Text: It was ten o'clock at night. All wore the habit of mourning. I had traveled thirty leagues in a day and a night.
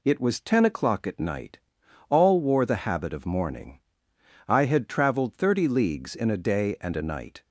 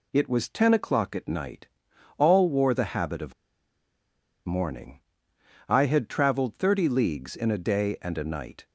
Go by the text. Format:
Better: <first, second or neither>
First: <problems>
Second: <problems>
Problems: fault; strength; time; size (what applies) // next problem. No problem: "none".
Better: first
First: none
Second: pauses between "of" and "mourning"; at 3.3 s; 1.1 s long